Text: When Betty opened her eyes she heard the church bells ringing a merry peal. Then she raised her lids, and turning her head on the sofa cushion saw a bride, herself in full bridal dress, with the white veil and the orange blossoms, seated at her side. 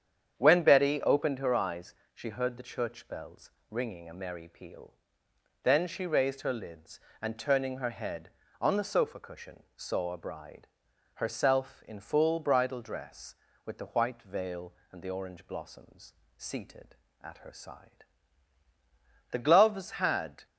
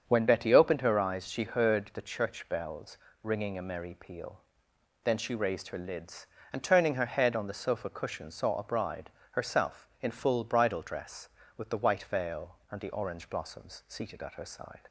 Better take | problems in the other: second | starts louder than the rest; strong; until 1.4 s; 8.5 dB; strong in the second // pauses between "eyes" and "she"; slight; at 1.9 s; 0.20 s long // pauses between "bells" and "ringing"; slight; at 3.5 s; 0.18 s long; slight in the second // goes on to say "The gloves had"; noticeable; from 19.3 s on; 1.1 s long

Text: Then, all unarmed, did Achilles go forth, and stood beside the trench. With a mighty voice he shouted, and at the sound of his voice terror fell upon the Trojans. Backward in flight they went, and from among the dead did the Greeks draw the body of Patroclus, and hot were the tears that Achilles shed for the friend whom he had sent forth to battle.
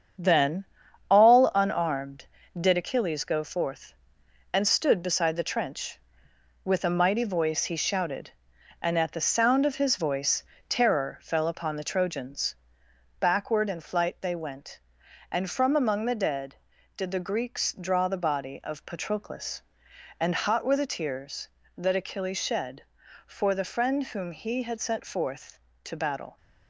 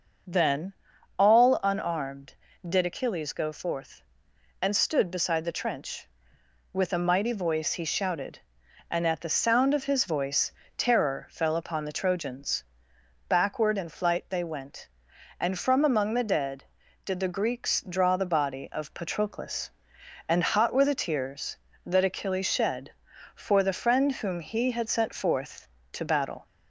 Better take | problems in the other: second | gets quieter; throughout; 7 dB // pauses between "voice" and "terror"; slight; at 10.4 s; 0.26 s long; slight in the second

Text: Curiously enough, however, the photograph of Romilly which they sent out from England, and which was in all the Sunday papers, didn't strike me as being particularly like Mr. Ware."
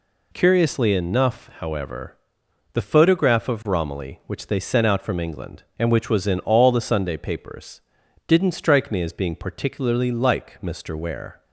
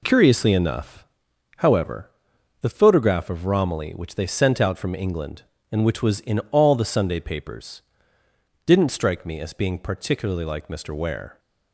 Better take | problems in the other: neither | none

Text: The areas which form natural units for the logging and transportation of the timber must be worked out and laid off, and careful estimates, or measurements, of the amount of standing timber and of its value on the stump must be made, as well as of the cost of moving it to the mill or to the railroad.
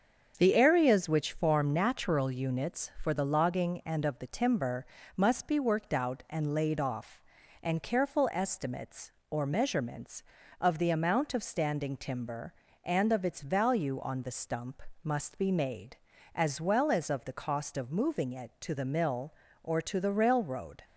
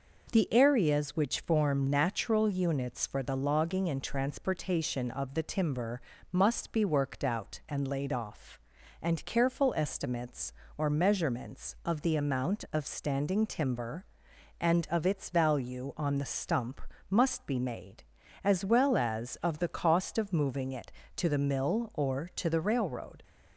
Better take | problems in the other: second | starts louder than the rest; until 1.3 s; 7 dB // skips "transportation"; at 4.0 s // pauses between "timber" and "must"; slight; at 4.8 s; 0.30 s long; slight in the second // pauses between "stump" and "must"; slight; at 14.8 s; 0.22 s long; slight in the second

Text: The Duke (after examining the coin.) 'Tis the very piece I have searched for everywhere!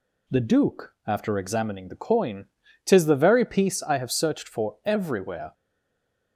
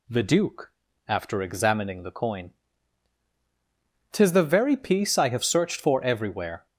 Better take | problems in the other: second | stays silent after the last word; slight; from 5.5 s on; 0.8 s long

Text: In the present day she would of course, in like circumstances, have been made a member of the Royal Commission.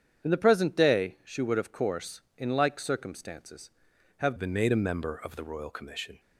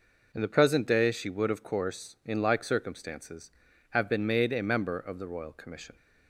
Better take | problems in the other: second | starts louder than the rest; strong; until 1.3 s; 8.5 dB // changes voice at "been"; from 4.3 s on; 1.8 s long

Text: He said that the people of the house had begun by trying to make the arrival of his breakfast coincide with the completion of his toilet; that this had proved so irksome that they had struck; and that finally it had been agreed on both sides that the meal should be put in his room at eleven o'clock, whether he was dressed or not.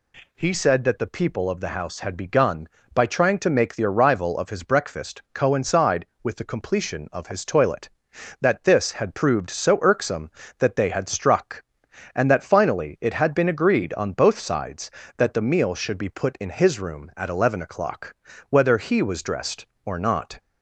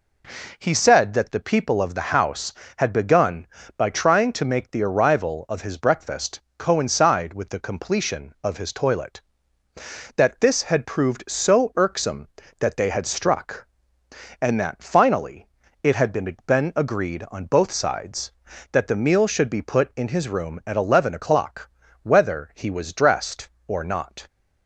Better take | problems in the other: first | pauses between "breakfast" and "coincide"; slight; at 6.3 s; 0.18 s long // pauses between "finally" and "it"; at 15.4 s; 0.38 s long // says "been" twice; at 16.4 s

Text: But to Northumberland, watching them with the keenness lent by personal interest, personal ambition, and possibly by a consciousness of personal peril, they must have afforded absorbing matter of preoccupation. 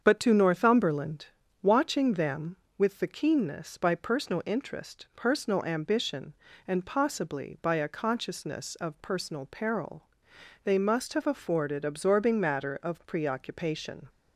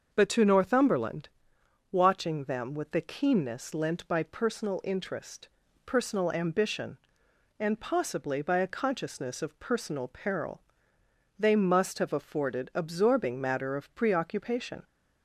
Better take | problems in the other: second | starts louder than the rest; strong; until 1.0 s; 7.5 dB; also in the second // skips "lent"; at 3.7 s

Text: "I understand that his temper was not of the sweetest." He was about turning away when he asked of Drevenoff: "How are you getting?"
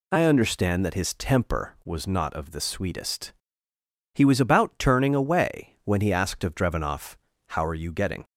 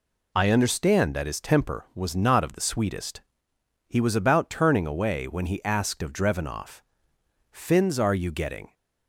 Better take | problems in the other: first | says "Fins" for "How"; at 7.4 s

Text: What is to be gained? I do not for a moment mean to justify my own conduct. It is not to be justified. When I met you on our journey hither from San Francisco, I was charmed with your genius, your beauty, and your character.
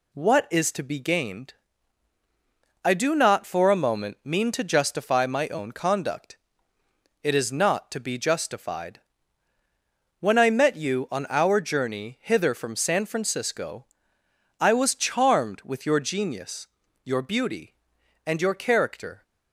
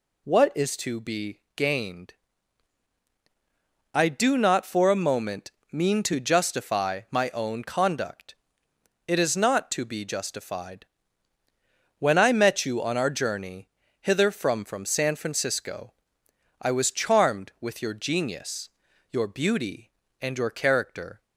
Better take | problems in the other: first | pauses between "be" and "gained"; slight; at 1.3 s; 0.18 s long // pauses between "moment" and "mean"; slight; at 5.5 s; 0.18 s long // pauses between "journey" and "hither"; slight; at 13.6 s; 0.32 s long // says "from" twice; at 14.6 s

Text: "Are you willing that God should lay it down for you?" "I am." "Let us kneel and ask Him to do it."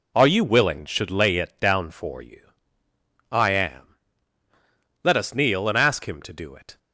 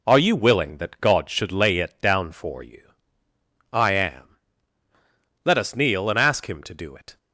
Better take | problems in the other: second | skips "that God"; at 0.8 s

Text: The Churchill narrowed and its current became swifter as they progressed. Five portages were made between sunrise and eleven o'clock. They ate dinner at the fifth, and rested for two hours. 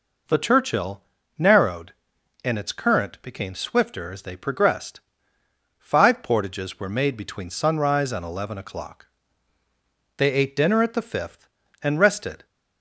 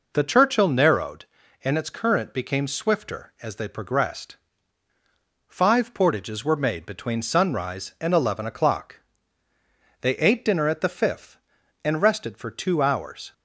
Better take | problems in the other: second | pauses between "Churchill" and "narrowed"; slight; at 1.0 s; 0.34 s long // stops before "for two hours"; at 12.4 s

